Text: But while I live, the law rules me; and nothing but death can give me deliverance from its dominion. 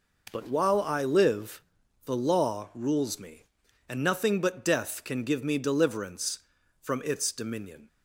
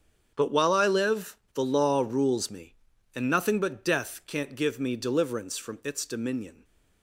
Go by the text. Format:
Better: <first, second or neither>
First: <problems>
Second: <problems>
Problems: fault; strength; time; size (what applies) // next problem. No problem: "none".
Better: first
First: none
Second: starts louder than the rest; strong; until 1.3 s; 7.5 dB // says "can't" for "can"; at 4.2 s